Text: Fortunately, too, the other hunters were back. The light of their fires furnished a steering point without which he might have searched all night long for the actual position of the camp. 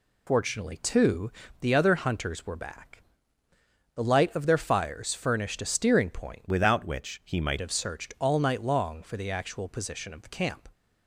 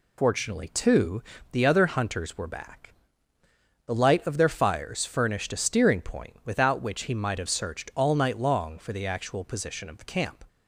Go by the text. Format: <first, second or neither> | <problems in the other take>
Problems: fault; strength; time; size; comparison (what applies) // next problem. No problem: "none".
second | changes voice from "without" to "might"; from 6.4 to 7.5 s; 1.1 s long